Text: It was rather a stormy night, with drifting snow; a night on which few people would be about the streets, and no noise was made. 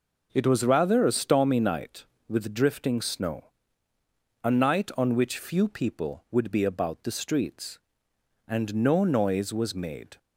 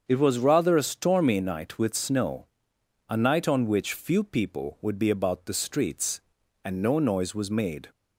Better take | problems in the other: first | starts louder than the rest; until 1.0 s; 7 dB // skips "drifting"; at 1.9 s

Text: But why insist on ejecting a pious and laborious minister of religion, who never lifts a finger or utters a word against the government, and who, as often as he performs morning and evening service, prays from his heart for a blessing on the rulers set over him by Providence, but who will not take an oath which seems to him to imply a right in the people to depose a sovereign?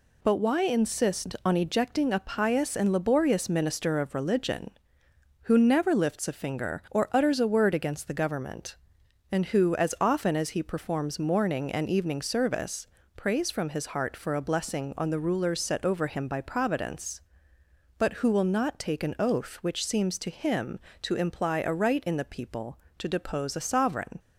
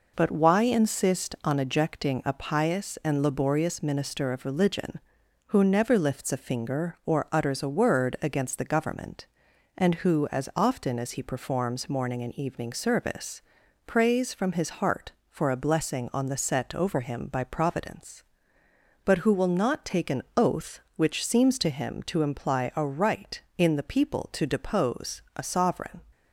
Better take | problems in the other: first | skips "rulers"; at 16.3 s

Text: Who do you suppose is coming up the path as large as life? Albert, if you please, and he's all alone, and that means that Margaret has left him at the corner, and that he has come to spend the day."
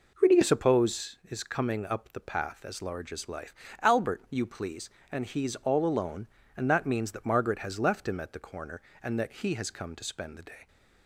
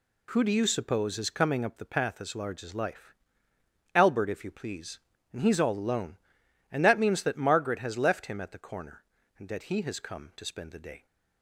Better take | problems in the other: second | skips "if"; at 4.2 s

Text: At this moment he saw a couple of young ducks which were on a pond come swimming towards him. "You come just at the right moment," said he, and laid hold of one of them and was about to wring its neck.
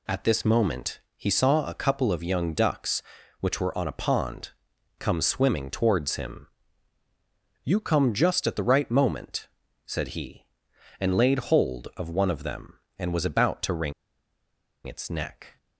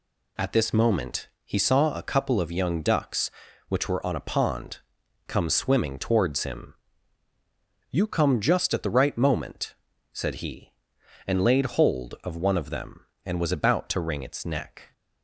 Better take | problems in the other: second | pauses between "moment" and "he"; slight; at 0.9 s; 0.16 s long; slight in the second // pauses between "pond" and "come"; noticeable; at 4.4 s; 0.50 s long; noticeable in the second // pauses between "wring" and "its"; noticeable; at 13.9 s; 0.94 s long

